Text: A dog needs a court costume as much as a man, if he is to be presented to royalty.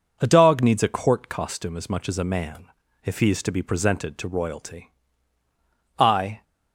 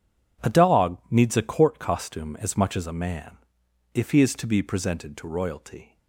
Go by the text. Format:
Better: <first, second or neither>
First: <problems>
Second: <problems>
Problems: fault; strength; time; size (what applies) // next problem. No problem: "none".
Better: second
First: goes on to say "I"; slight; from 5.9 s on; 0.46 s long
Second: none